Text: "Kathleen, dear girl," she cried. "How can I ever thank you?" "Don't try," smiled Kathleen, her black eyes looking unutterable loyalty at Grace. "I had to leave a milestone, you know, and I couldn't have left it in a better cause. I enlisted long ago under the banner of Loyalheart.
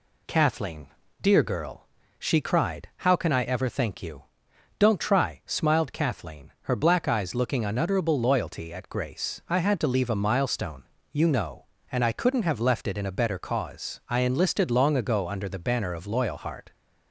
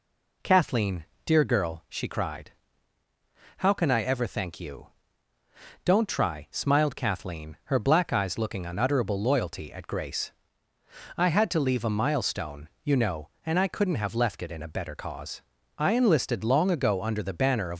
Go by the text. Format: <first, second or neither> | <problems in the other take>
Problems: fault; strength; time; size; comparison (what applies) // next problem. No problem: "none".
first | stops before "Loyalheart"; at 17.7 s